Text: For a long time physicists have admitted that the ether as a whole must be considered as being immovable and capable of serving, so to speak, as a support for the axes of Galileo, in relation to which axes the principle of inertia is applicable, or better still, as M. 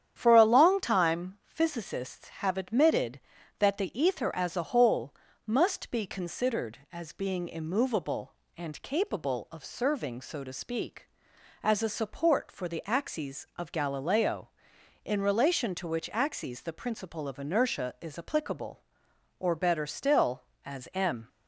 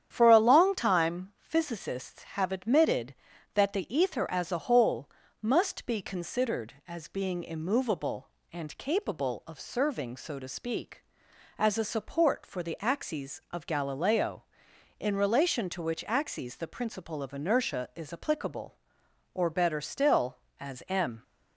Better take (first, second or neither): neither